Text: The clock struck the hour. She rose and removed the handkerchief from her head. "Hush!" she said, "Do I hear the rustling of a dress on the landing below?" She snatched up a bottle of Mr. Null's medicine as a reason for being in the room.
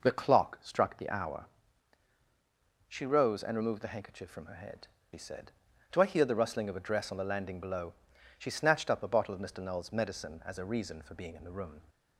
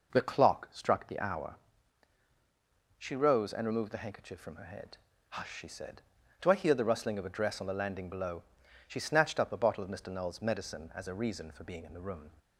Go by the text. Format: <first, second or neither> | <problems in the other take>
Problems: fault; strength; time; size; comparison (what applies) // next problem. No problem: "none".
second | skips "Hush"; at 4.9 s